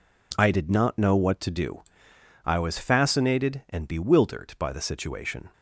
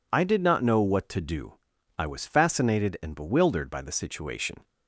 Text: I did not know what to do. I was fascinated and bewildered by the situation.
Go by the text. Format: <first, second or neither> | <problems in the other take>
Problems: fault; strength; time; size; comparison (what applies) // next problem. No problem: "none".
neither | none